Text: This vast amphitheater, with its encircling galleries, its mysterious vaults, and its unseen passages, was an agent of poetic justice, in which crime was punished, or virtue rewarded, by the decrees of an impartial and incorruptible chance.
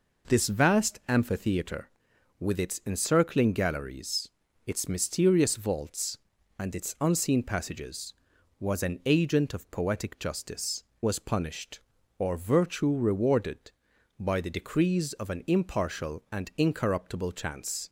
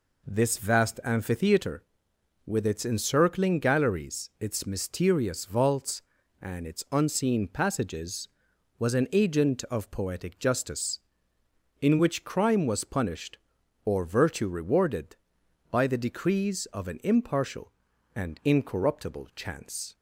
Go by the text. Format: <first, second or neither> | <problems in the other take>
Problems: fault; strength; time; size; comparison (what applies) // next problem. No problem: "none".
second | skips "in which crime"; at 10.9 s